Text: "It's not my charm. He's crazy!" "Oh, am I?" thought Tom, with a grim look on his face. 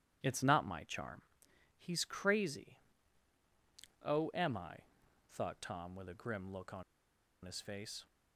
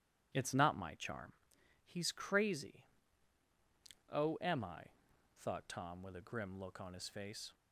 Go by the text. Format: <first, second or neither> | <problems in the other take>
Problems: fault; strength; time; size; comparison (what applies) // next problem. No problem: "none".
second | pauses between "on" and "his"; noticeable; at 6.8 s; 0.61 s long